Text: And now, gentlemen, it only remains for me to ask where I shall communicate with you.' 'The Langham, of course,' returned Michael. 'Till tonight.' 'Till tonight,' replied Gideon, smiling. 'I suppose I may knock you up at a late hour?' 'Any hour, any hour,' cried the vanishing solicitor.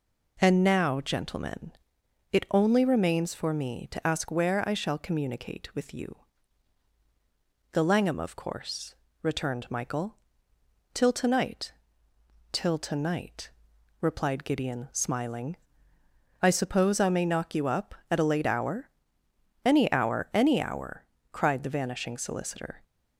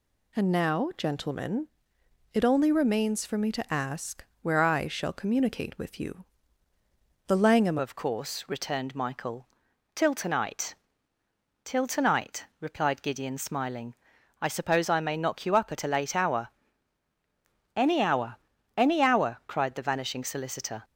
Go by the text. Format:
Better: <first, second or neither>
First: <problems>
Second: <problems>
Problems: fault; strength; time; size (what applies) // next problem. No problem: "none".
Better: first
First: none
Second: pauses between "ask" and "where"; slight; at 4.2 s; 0.20 s long // changes voice at "of"; from 7.7 s on; 13.1 s long